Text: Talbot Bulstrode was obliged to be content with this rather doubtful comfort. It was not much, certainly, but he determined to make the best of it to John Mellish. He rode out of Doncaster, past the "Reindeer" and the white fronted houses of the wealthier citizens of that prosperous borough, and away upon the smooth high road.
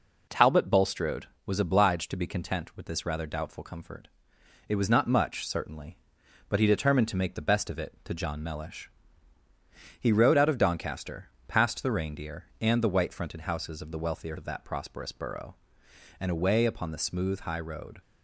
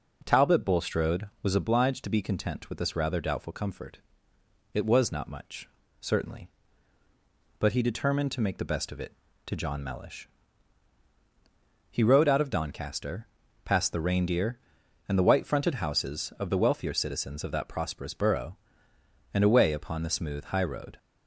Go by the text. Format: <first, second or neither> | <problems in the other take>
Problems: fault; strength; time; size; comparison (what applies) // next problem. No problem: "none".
second | skips "citizens"; at 14.3 s